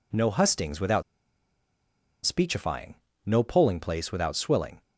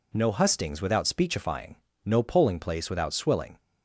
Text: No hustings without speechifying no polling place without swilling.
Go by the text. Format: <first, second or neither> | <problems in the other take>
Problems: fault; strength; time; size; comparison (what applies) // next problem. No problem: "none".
second | pauses between "without" and "speechifying"; at 1.0 s; 1.2 s long // pauses between "speechifying" and "no"; slight; at 2.9 s; 0.28 s long; slight in the second